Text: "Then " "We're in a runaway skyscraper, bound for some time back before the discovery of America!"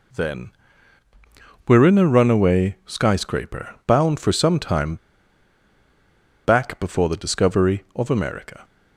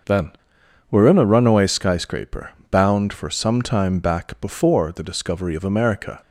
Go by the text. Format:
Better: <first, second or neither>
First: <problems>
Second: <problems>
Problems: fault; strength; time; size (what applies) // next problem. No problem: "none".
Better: second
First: pauses between "time" and "back"; strong; at 4.9 s; 1.4 s long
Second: none